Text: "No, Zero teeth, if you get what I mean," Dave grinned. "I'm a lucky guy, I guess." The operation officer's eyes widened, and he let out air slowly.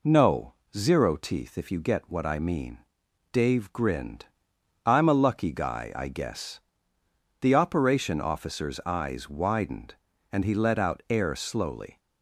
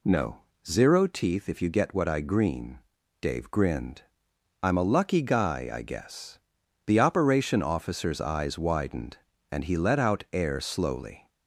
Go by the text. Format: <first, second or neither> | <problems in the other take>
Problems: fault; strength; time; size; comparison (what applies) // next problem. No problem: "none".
first | says "green" for "mean"; at 2.1 s